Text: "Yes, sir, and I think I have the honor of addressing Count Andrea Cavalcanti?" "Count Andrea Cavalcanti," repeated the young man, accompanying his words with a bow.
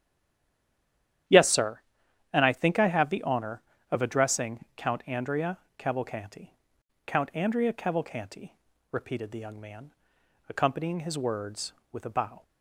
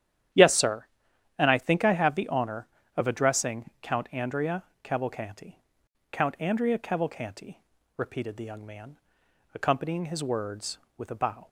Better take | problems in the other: second | stays silent before the first word; noticeable; until 1.2 s; 1.2 s long // starts louder than the rest; strong; until 2.8 s; 10.5 dB; strong in the second // pauses between "Andrea" and "Cavalcanti"; slight; at 5.5 s; 0.22 s long; slight in the second

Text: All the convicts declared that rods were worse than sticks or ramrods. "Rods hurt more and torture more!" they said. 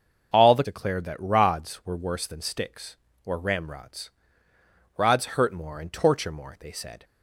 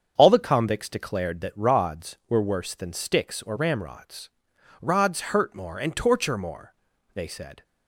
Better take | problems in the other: second | starts louder than the rest; noticeable; until 1.3 s; 6 dB; strong in the second // skips "convicts"; at 0.6 s

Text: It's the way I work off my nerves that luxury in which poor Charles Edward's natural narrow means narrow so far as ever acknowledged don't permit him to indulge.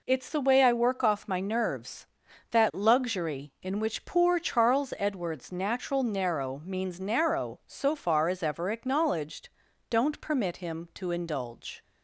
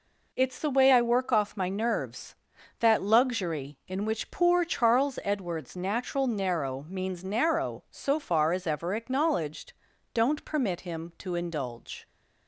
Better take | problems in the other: neither | pauses between "acknowledged" and "don't"; the same in both

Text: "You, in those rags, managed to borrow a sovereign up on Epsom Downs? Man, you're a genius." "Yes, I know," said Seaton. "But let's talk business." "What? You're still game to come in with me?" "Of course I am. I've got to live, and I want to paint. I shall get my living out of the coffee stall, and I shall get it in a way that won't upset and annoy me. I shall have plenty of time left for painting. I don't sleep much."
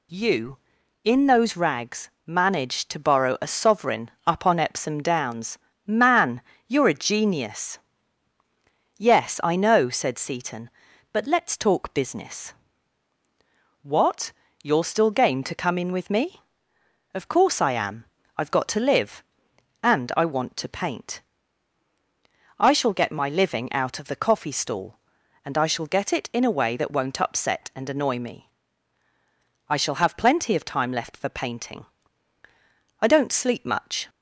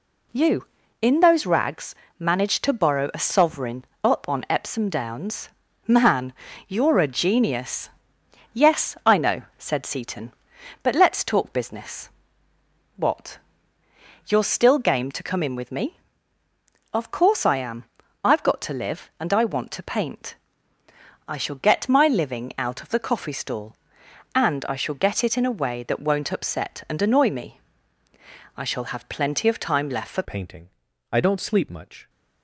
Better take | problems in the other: first | pauses between "sovereign" and "up"; slight; at 3.8 s; 0.18 s long; slight in the first // changes voice at "painting"; from 30.2 s on; 1.8 s long

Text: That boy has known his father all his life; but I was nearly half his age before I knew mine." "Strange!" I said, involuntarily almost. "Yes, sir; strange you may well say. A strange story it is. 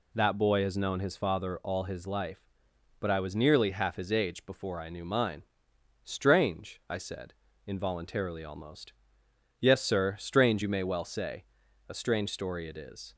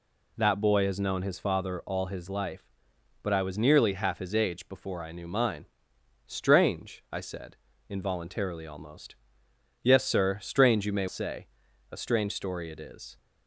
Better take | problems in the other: first | skips "well"; at 11.0 s

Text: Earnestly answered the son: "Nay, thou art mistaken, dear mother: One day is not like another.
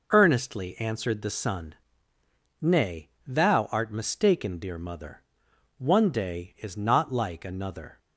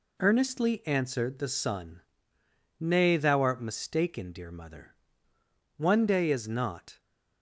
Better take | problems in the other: first | stops before "like another"; at 7.0 s

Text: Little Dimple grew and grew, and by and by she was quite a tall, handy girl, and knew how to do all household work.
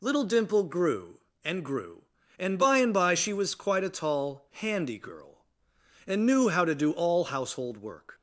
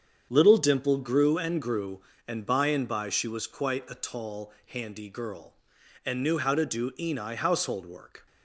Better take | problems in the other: first | starts louder than the rest; strong; until 1.3 s; 7.5 dB // says "eni" for "all"; at 6.9 s

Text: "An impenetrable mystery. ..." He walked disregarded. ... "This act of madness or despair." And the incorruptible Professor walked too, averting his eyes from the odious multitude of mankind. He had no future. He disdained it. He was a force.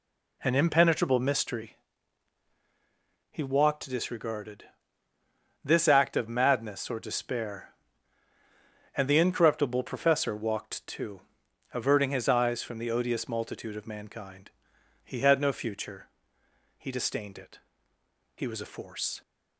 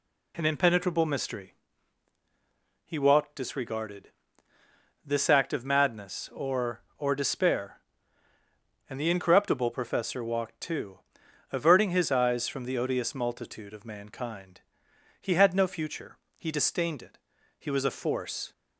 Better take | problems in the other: first | says "or" twice; at 6.9 s

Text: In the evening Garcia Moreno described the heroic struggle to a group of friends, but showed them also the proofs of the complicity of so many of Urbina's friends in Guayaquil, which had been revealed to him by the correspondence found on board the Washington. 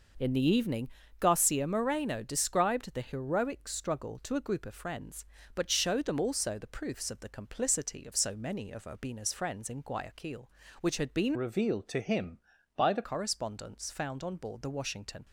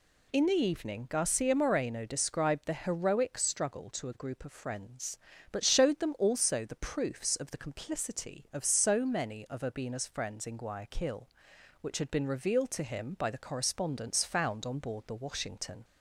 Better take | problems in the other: second | pauses between "evening" and "Garcia"; slight; at 0.8 s; 0.32 s long // changes voice from "revealed" to "the"; from 11.3 to 13.0 s; 1.7 s long

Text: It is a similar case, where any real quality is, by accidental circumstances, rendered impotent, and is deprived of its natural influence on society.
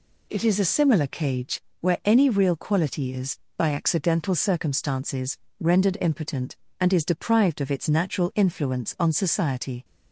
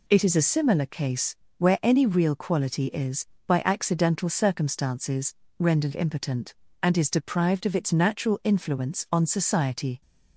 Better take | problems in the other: second | says "cage" for "case"; at 1.0 s

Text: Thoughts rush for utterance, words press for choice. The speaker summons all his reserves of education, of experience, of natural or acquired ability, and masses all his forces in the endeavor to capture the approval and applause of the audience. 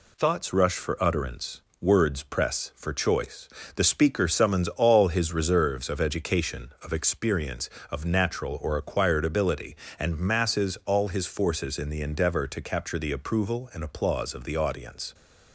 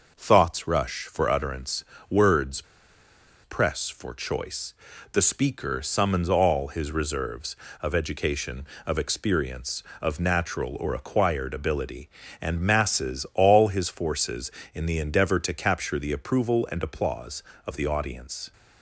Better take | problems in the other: first | pauses between "words" and "press"; noticeable; at 2.6 s; 0.81 s long

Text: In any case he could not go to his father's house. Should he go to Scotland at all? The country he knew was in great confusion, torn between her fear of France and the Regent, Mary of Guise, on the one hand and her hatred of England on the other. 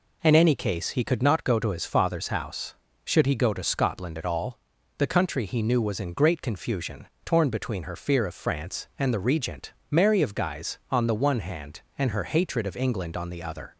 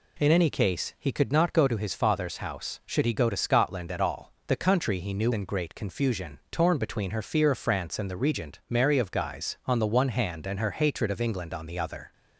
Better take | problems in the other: first | skips "was"; at 5.3 s

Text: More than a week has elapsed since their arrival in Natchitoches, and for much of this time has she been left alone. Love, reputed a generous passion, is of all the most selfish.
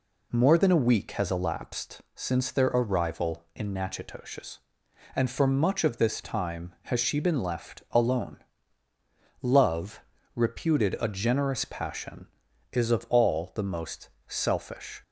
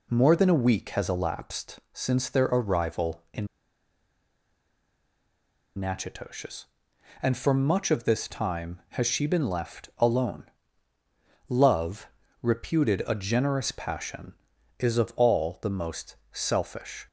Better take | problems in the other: first | pauses between "in" and "Natchitoches"; strong; at 3.4 s; 2.3 s long // pauses between "most" and "selfish"; slight; at 16.1 s; 0.16 s long; slight in the first

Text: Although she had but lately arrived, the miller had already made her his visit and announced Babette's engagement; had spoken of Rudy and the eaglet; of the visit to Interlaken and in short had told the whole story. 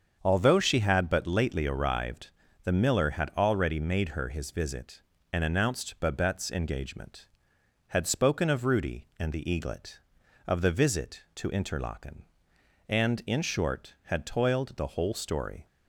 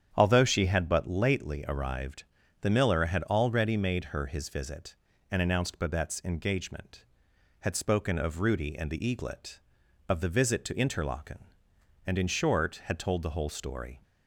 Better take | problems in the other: second | starts louder than the rest; strong; until 1.2 s; 7 dB; strong in the second // says "toiled" for "told"; at 14.2 s

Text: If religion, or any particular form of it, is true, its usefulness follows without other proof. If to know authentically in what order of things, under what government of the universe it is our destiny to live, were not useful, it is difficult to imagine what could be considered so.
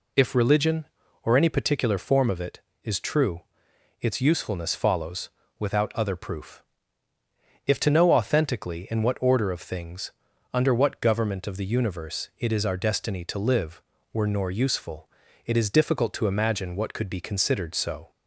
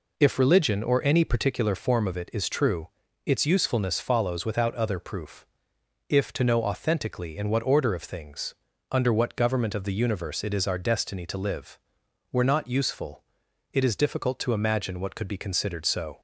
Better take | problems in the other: second | pauses between "follows" and "without"; slight; at 5.2 s; 0.30 s long // says "nor" for "not"; at 14.2 s

